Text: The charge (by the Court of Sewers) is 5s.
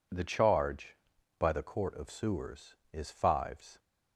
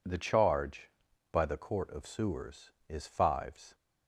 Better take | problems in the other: neither | none

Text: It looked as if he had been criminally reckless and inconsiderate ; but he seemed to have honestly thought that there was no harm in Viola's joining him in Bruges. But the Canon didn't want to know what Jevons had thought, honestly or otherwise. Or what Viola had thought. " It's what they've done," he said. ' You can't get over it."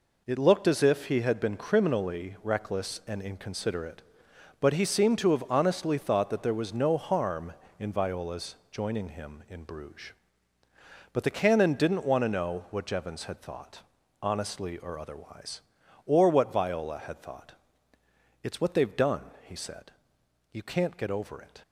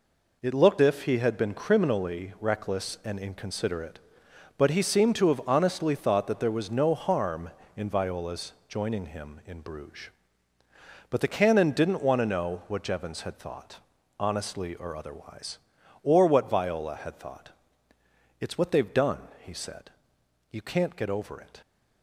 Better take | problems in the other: first | skips "as"; at 0.8 s // pauses between "Viola's" and "joining"; slight; at 8.5 s; 0.16 s long; slight in the first

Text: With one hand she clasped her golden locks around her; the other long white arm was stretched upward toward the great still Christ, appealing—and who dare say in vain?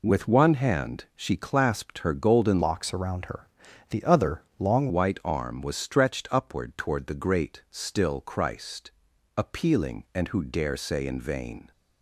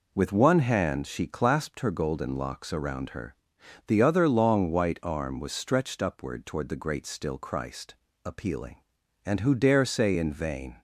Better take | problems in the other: second | changes voice from "locks" to "long"; from 2.6 to 4.8 s; 2.2 s long // pauses between "other" and "long"; slight; at 4.4 s; 0.16 s long

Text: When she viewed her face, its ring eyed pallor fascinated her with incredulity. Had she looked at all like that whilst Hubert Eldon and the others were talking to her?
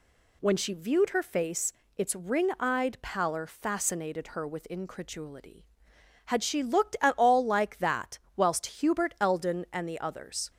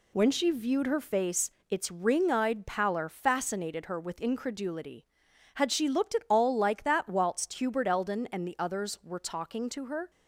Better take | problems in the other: second | pauses between "that" and "whilst"; slight; at 8.1 s; 0.18 s long // stops before "were talking to her"; at 10.4 s

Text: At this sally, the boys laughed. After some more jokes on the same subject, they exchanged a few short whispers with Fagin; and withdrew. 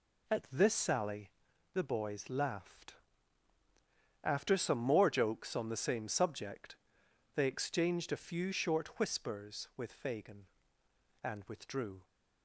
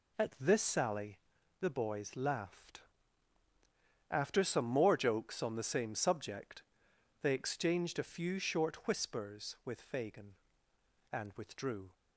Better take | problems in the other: neither | none

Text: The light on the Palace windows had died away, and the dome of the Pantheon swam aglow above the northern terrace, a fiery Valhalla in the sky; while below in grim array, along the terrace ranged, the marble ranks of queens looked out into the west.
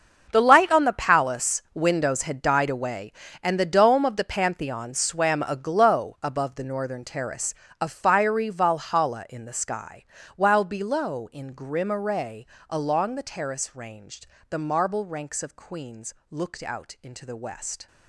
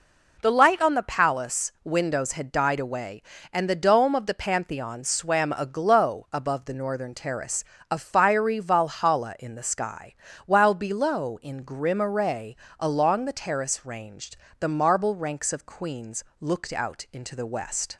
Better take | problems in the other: second | gets quieter; strong; throughout; 14 dB // pauses between "queens" and "looked"; slight; at 16.1 s; 0.16 s long; slight in the second

